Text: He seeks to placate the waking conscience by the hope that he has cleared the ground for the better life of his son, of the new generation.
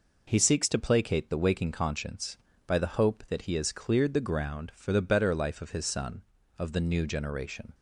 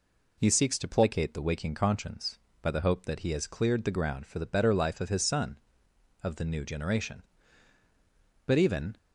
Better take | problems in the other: first | goes on to say "But even"; from 8.4 s on; 0.52 s long

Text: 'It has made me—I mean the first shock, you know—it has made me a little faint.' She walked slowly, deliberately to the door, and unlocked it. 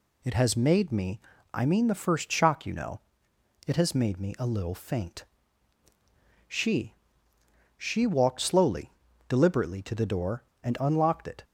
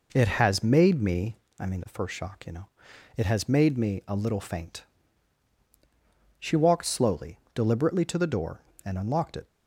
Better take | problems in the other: second | says "She" twice; at 7.7 s

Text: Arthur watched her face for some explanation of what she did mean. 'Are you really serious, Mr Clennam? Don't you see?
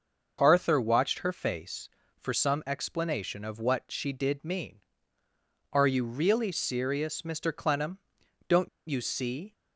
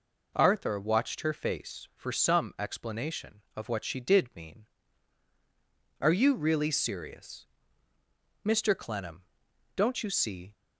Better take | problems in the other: second | starts louder than the rest; noticeable; until 1.4 s; 6 dB // pauses between "Don't" and "you"; slight; at 8.6 s; 0.20 s long

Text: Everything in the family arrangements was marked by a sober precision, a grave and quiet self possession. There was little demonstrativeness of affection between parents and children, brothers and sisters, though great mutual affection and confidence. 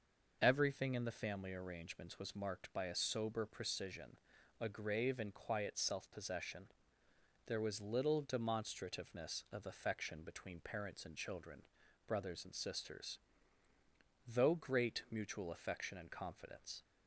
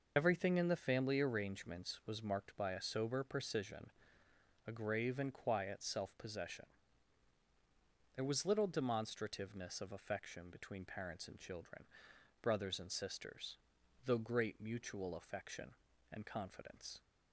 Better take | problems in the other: first | loses the start of "Everything"; at 0.1 s; 70 ms

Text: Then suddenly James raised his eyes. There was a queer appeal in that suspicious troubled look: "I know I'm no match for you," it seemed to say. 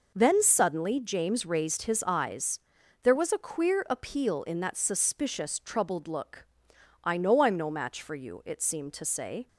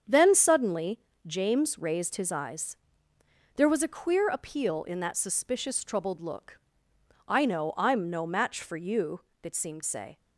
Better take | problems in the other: first | starts louder than the rest; strong; until 1.3 s; 7.5 dB // pauses between "suddenly" and "James"; slight; at 0.9 s; 0.26 s long // skips "to"; at 9.8 s

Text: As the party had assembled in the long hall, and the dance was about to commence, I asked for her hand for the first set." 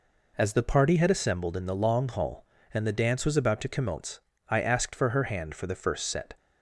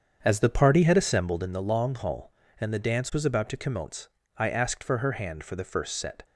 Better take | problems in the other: first | starts louder than the rest; strong; until 1.6 s; 7.5 dB

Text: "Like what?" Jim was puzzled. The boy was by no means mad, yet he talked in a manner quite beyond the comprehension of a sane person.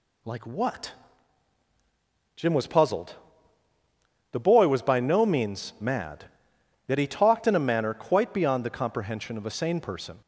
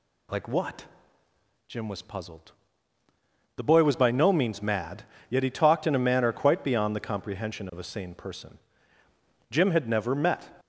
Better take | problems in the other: first | goes on to say "Jim had never met"; noticeable; from 9.5 s on; 0.98 s long

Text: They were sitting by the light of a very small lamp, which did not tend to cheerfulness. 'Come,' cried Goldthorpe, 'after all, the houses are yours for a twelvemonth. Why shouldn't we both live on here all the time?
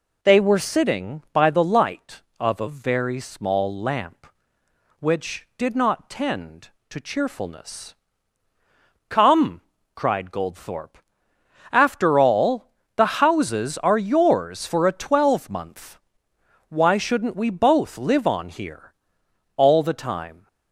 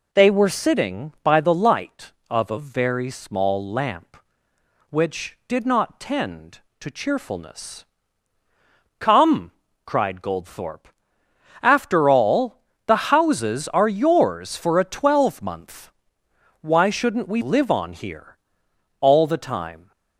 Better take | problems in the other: first | skips "both"; at 17.4 s // pauses between "here" and "all"; noticeable; at 18.3 s; 0.64 s long; noticeable in the first

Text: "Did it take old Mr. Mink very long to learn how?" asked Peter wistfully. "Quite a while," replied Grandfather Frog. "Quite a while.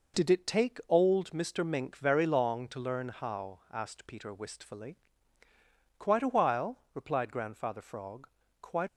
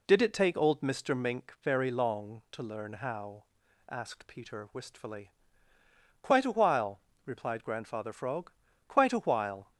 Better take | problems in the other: second | stops before "a while"; at 8.8 s

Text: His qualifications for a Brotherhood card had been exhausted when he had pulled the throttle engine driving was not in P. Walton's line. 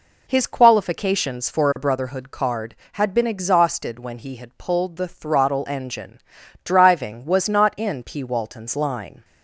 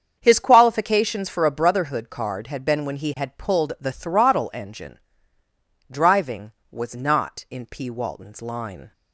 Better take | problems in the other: first | starts louder than the rest; strong; until 1.2 s; 7.5 dB // skips "exhausted"; at 2.8 s // pauses between "engine" and "driving"; noticeable; at 4.9 s; 0.92 s long; also in the first

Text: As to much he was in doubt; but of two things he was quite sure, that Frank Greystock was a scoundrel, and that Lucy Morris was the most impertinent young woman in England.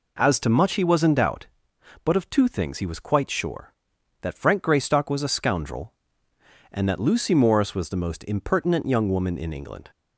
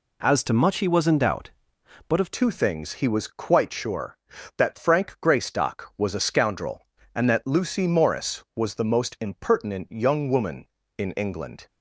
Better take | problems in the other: first | changes voice at "two"; from 2.3 s on; 9.3 s long

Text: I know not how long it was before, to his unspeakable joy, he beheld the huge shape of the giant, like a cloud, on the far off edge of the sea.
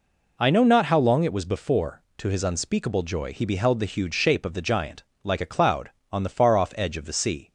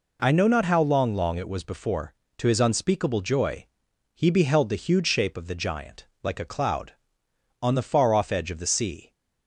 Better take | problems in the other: first | says "long" twice; at 1.1 s

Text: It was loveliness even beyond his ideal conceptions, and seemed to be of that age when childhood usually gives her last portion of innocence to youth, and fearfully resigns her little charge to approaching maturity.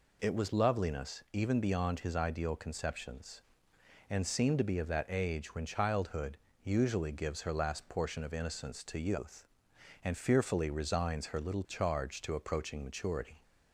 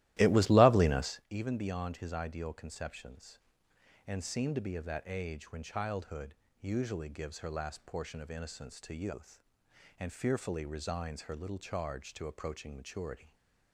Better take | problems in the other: first | starts louder than the rest; strong; until 1.3 s; 15.5 dB // pauses between "childhood" and "usually"; slight; at 6.3 s; 0.26 s long; slight in the first

